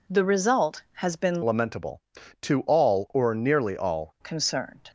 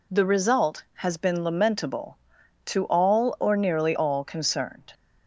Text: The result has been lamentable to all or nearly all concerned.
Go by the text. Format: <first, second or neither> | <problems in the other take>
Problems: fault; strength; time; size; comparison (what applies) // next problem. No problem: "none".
second | changes voice from "lamentable" to "all"; from 1.4 to 4.1 s; 2.7 s long